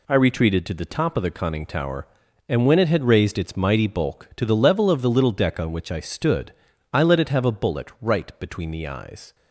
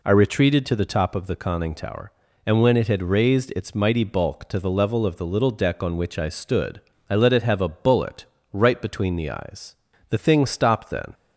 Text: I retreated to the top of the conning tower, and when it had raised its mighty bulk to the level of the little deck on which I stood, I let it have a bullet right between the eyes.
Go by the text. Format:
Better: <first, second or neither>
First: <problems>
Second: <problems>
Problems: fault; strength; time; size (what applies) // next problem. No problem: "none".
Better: first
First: none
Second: pauses between "bullet" and "right"; slight; at 8.2 s; 0.30 s long // goes on to say "The thing stopped then"; noticeable; from 10.0 s on; 1.0 s long